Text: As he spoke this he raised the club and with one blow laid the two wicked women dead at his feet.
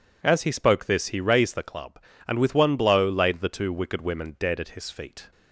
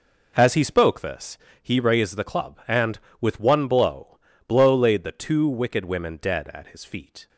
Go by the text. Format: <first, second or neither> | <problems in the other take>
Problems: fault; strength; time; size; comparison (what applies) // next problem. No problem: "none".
first | pauses between "this" and "he"; slight; at 1.3 s; 0.24 s long // says "blow" twice; at 4.4 s